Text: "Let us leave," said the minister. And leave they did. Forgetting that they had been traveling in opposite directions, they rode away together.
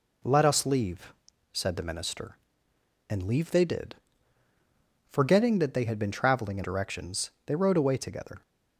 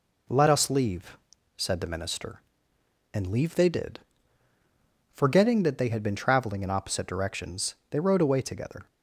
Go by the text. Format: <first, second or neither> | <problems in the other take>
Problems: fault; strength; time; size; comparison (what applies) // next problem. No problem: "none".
second | skips "opposite"; at 6.6 s